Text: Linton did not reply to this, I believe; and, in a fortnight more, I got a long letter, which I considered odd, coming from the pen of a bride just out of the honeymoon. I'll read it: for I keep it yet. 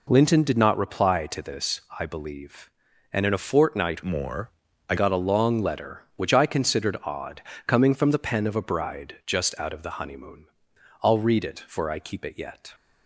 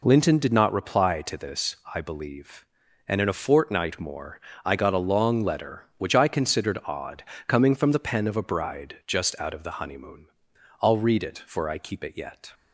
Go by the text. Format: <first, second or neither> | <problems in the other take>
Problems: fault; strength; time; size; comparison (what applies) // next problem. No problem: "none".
second | changes voice from "more" to "I"; from 4.0 to 4.9 s; 0.9 s long